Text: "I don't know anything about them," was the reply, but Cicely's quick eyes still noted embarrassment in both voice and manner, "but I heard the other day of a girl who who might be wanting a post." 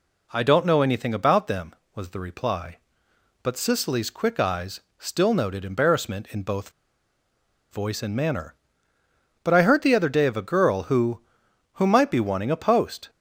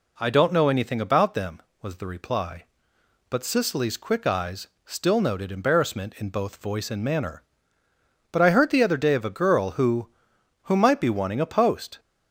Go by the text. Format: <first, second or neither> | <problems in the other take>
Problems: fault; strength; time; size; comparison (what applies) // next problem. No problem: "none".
second | pauses between "eyes" and "still"; slight; at 4.8 s; 0.18 s long; slight in the second // pauses between "both" and "voice"; at 6.7 s; 1.0 s long